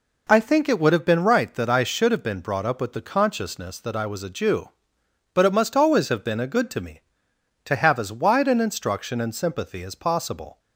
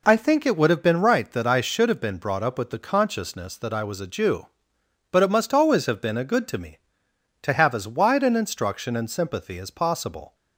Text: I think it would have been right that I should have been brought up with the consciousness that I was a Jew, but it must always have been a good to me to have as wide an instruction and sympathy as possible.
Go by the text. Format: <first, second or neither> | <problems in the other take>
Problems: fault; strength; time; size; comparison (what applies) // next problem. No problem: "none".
neither | none